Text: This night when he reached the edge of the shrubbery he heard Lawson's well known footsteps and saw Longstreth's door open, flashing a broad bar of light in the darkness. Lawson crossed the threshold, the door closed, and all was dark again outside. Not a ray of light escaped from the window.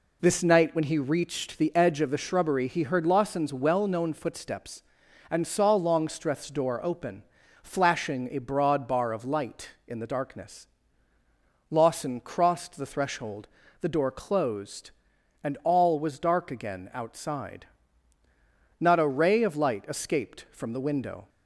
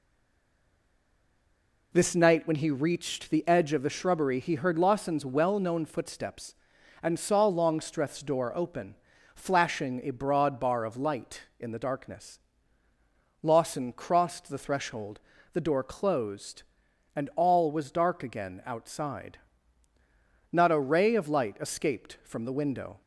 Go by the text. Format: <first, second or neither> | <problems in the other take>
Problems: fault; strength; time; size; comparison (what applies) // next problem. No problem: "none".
first | stays silent before the first word; noticeable; until 1.9 s; 1.9 s long